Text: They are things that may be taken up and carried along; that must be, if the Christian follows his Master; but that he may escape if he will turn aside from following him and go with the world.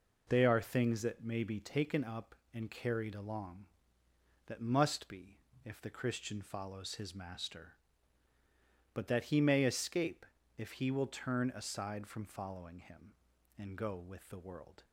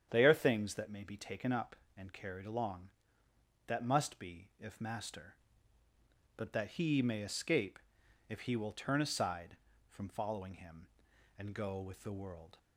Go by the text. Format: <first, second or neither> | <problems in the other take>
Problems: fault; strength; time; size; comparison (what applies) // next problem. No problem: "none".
first | starts louder than the rest; strong; until 1.1 s; 8.5 dB // skips "the Christian follows his"; at 4.7 s // pauses between "escape" and "if"; noticeable; at 7.7 s; 0.50 s long; slight in the first